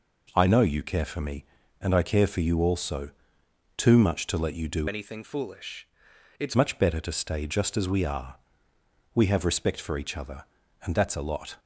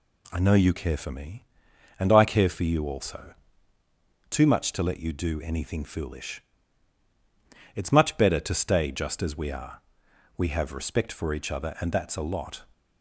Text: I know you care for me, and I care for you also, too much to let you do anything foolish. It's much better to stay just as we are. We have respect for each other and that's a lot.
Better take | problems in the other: second | changes voice from "anything" to "It's"; from 4.8 to 6.5 s; 1.7 s long

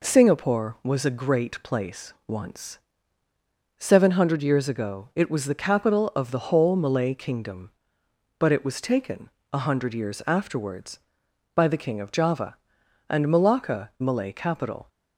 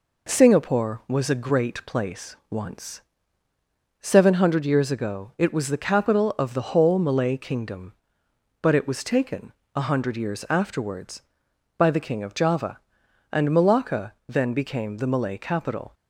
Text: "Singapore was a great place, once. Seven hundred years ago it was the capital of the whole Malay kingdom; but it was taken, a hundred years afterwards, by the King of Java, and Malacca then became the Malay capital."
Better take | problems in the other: second | skips "then became the"; at 13.9 s

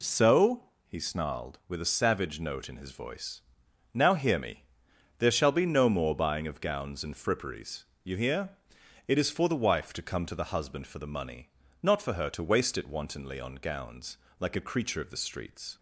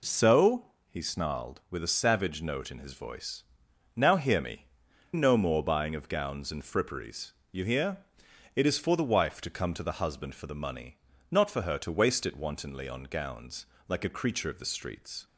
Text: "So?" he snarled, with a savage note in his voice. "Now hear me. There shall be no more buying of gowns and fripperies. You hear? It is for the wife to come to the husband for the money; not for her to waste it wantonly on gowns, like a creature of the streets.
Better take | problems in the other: first | skips "There shall be"; at 4.8 s

